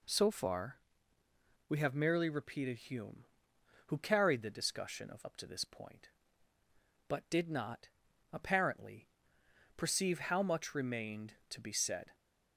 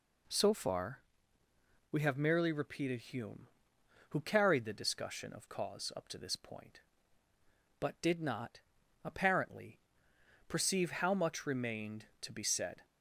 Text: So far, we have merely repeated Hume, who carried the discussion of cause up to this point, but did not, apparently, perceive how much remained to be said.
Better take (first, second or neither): second